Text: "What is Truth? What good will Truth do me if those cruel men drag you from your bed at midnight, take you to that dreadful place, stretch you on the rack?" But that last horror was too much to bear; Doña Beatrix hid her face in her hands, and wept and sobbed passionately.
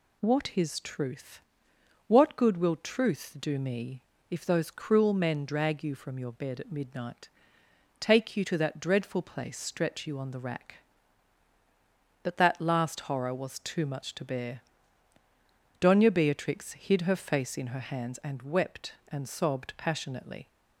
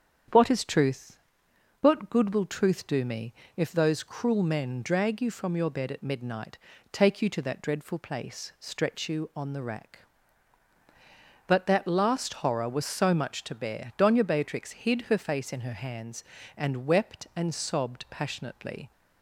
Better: first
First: pauses between "me" and "if"; slight; at 4.0 s; 0.26 s long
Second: starts louder than the rest; strong; until 1.9 s; 8.5 dB // pauses between "me" and "if"; slight; at 3.3 s; 0.24 s long // says "so" for "too"; at 12.8 s

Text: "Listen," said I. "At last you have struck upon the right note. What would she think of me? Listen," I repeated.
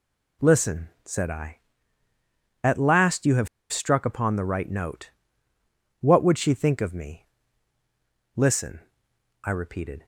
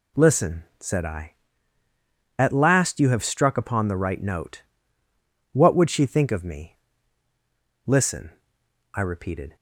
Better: second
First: pauses between "have" and "struck"; slight; at 3.4 s; 0.24 s long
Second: none

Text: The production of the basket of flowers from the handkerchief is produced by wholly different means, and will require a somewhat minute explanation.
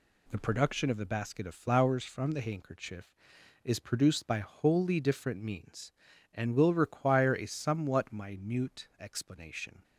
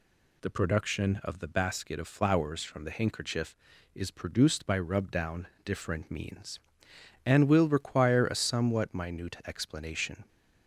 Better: first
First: none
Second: says "rubdown" for "wholly"; at 4.7 s

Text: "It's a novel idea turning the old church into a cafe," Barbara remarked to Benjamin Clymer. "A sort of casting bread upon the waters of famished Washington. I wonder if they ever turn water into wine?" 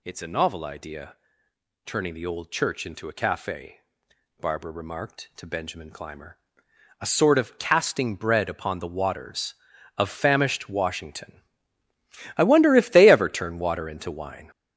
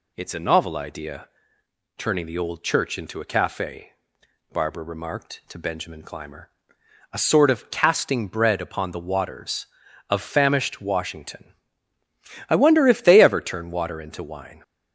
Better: second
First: gets louder; strong; throughout; 8 dB // pauses between "idea" and "turning"; noticeable; at 1.1 s; 0.70 s long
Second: pauses between "idea" and "turning"; noticeable; at 1.2 s; 0.70 s long

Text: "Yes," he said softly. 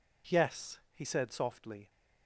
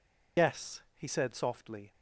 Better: first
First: none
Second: loses the start of "Yes"; at 0.3 s; 100 ms

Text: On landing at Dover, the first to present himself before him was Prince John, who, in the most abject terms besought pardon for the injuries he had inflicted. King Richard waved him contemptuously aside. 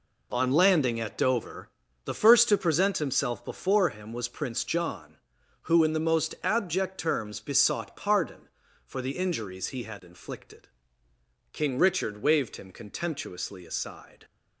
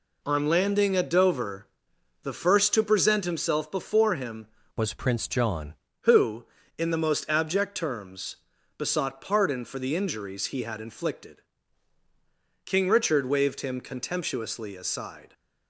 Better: first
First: none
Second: changes voice from "was" to "John"; from 4.7 to 5.7 s; 1.0 s long // pauses between "terms" and "besought"; at 8.3 s; 0.42 s long

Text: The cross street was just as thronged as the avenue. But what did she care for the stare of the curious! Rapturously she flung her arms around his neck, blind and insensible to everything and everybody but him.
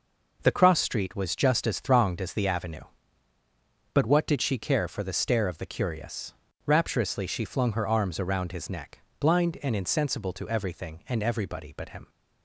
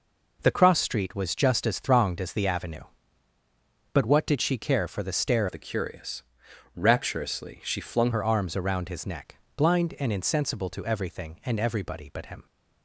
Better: first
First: none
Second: changes voice from "of" to "flung"; from 5.4 to 8.1 s; 2.7 s long

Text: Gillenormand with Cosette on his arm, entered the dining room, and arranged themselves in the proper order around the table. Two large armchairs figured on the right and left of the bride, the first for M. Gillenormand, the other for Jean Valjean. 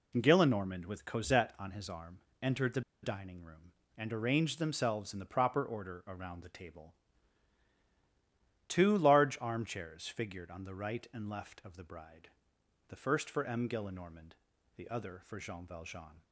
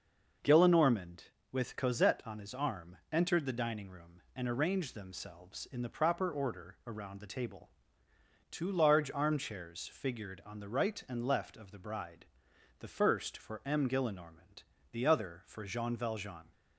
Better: second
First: pauses between "the" and "dining"; slight; at 2.8 s; 0.22 s long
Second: none

